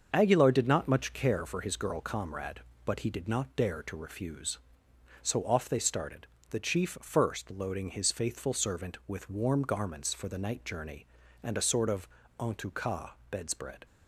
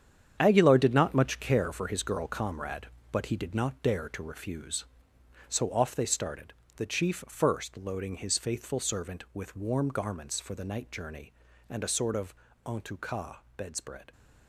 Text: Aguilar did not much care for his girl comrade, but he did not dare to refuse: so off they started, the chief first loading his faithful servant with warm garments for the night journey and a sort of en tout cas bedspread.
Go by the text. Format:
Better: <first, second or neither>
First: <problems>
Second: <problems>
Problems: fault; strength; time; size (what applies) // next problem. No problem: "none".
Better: first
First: starts louder than the rest; until 1.1 s; 6.5 dB // pauses between "of" and "en"; slight; at 12.0 s; 0.32 s long // pauses between "cas" and "bedspread"; slight; at 13.0 s; 0.22 s long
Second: gets quieter; strong; throughout; 10.5 dB // starts louder than the rest; strong; until 1.4 s; 8.5 dB // pauses between "of" and "en"; slight; at 12.3 s; 0.32 s long // pauses between "cas" and "bedspread"; slight; at 13.3 s; 0.22 s long